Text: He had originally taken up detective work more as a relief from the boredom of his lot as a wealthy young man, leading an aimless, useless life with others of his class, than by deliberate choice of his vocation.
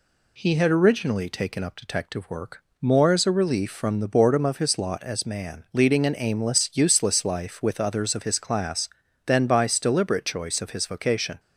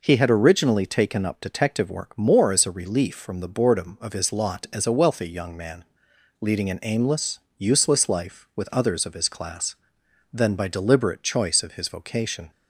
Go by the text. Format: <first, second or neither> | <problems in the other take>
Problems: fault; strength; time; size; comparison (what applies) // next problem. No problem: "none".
second | pauses between "work" and "more"; slight; at 2.6 s; 0.16 s long // skips "a wealthy young"; at 5.2 s